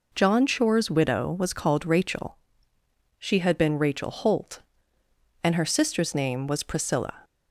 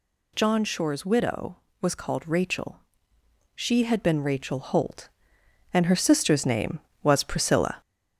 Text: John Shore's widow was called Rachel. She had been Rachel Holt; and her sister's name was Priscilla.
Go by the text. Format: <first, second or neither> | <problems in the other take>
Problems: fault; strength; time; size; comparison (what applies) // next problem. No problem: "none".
first | gets louder; slight; throughout; 3.5 dB